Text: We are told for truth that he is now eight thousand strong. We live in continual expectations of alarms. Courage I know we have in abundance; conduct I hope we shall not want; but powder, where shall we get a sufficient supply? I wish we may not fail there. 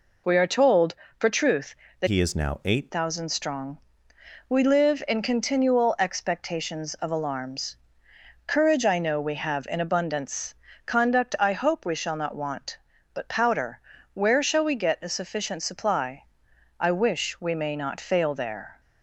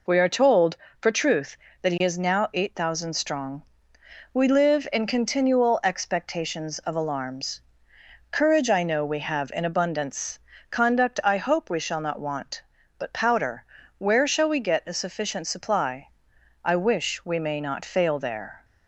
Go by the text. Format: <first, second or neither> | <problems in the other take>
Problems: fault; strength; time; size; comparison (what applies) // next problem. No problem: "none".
second | changes voice from "he" to "eight"; from 2.0 to 2.9 s; 0.9 s long